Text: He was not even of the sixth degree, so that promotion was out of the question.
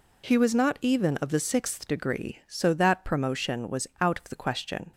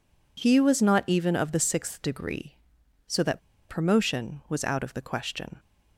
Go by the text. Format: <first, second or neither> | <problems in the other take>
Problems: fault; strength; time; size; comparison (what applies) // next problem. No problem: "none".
first | pauses between "that" and "promotion"; slight; at 3.3 s; 0.29 s long